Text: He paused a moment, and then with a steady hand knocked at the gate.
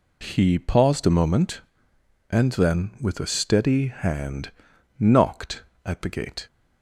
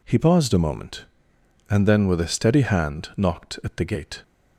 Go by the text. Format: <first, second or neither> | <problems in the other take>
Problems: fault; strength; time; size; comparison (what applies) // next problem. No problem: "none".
second | loses the start of "He"; at 0.2 s; 65 ms // pauses between "hand" and "knocked"; at 4.5 s; 0.44 s long